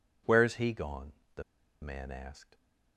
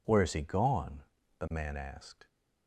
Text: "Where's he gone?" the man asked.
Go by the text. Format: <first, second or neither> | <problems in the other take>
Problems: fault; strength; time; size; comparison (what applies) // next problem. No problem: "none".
second | pauses between "the" and "man"; at 1.4 s; 0.40 s long